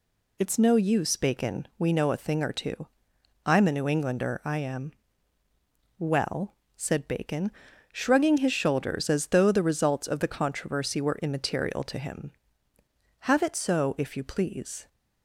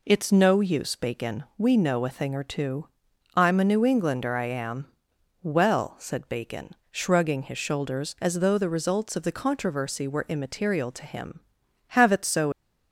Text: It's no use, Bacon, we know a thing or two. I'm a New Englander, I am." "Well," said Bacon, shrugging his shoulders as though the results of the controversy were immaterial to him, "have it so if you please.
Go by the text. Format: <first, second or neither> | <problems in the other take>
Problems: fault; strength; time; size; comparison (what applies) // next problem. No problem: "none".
first | stops before "if you please"; at 12.5 s